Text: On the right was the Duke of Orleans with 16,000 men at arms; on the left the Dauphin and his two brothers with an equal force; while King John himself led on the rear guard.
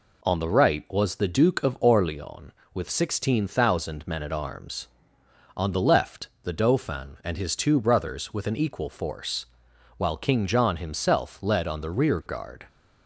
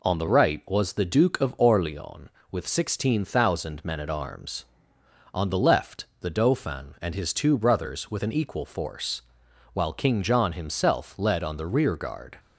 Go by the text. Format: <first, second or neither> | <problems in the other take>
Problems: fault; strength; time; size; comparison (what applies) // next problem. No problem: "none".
neither | pauses between "left" and "the"; slight; the same in both